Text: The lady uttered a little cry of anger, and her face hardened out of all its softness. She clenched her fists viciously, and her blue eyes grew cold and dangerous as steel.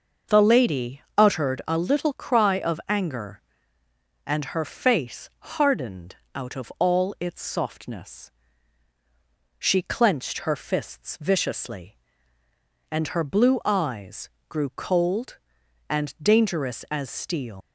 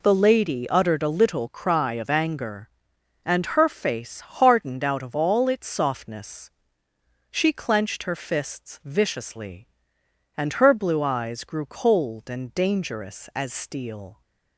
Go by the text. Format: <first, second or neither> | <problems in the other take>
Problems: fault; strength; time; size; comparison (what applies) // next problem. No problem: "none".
second | starts louder than the rest; noticeable; until 1.4 s; 6 dB // pauses between "lady" and "uttered"; slight; at 1.0 s; 0.16 s long // pauses between "hardened" and "out"; slight; at 6.1 s; 0.20 s long // pauses between "eyes" and "grew"; slight; at 14.3 s; 0.18 s long // leaves "steel" unfinished; at 17.6 s; 140 ms